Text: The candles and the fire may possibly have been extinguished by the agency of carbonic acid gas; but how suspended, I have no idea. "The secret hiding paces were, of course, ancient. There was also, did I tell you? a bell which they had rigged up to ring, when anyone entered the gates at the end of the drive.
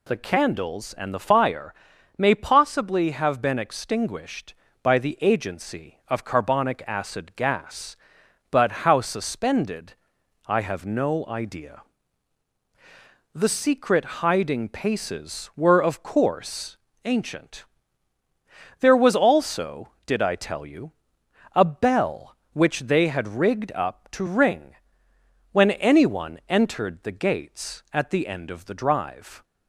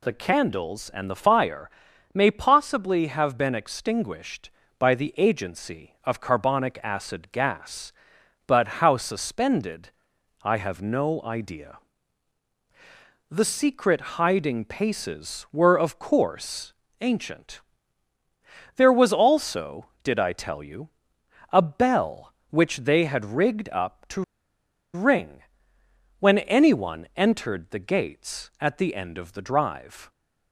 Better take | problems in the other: first | pauses between "fire" and "may"; at 1.6 s; 0.44 s long; also in the first // pauses between "but" and "how"; slight; at 8.6 s; 0.16 s long; slight in the first // pauses between "to" and "ring"; noticeable; at 24.2 s; 0.72 s long

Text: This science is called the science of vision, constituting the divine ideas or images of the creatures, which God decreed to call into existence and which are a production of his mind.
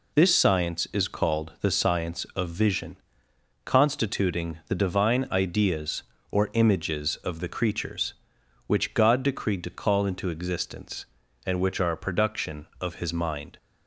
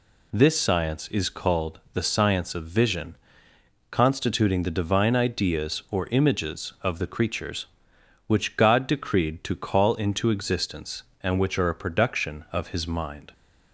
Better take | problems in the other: neither | none

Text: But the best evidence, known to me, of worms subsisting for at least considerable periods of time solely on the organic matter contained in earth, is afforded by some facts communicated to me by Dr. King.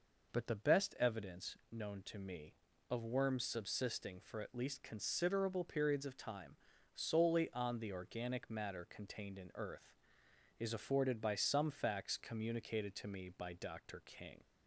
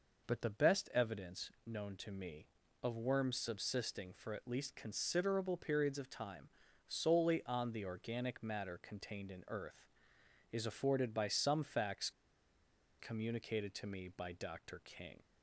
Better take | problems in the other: first | pauses between "time" and "solely"; at 6.4 s; 0.38 s long; also in the first // pauses between "facts" and "communicated"; noticeable; at 12.0 s; 0.89 s long

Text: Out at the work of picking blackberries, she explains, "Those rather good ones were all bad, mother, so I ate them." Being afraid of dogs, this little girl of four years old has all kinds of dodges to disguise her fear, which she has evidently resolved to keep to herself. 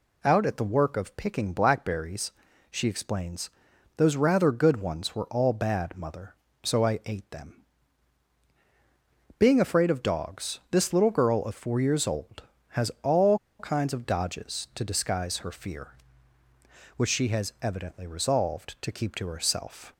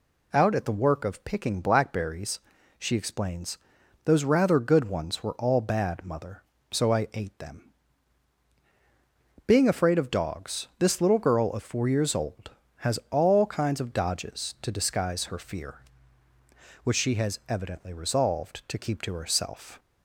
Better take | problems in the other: second | pauses between "all" and "kinds"; slight; at 13.3 s; 0.21 s long

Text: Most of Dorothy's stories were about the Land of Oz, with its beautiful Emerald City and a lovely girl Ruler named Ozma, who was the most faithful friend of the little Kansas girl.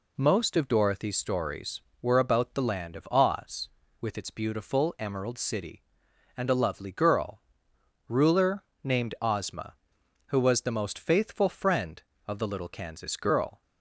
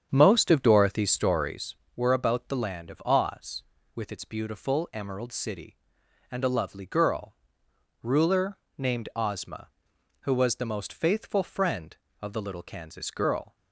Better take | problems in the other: first | starts louder than the rest; strong; until 1.6 s; 8 dB // pauses between "girl" and "Ruler"; noticeable; at 7.3 s; 0.68 s long; noticeable in the first // pauses between "Ruler" and "named"; slight; at 8.5 s; 0.22 s long; slight in the first

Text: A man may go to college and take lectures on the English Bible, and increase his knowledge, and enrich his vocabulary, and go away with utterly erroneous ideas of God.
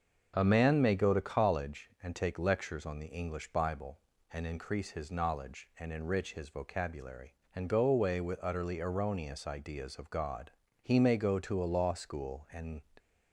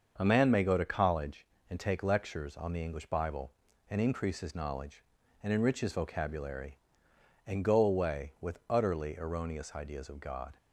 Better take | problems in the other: second | starts louder than the rest; until 1.3 s; 6.5 dB; also in the second // goes on to say "He may go to a law school and"; strong; from 10.8 s on; 1.9 s long

